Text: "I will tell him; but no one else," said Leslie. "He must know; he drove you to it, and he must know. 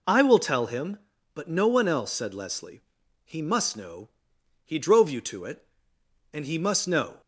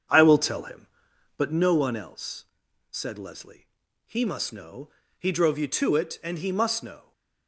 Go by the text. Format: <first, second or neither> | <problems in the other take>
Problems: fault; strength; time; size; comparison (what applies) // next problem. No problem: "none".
first | starts louder than the rest; until 1.6 s; 7 dB